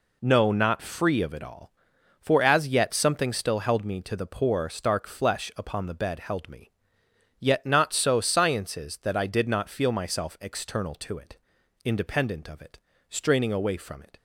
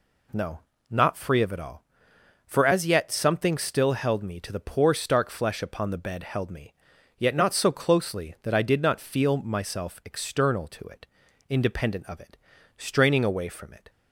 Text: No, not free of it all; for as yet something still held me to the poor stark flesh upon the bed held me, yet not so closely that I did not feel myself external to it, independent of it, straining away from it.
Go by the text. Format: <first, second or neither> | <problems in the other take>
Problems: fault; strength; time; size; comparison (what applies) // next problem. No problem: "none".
second | says "sciences" for "closely"; at 8.2 s